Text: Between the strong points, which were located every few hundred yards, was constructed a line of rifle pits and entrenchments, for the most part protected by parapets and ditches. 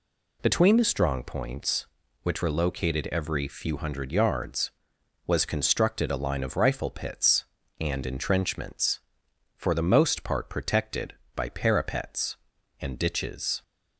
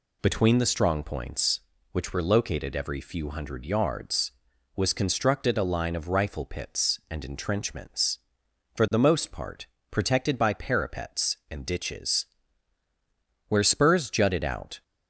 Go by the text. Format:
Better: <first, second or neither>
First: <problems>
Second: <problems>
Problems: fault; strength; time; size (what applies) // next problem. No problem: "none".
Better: first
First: none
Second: pauses between "part" and "protected"; slight; at 9.6 s; 0.24 s long // goes on to say "Where spurs jutted out"; from 13.4 s on; 1.3 s long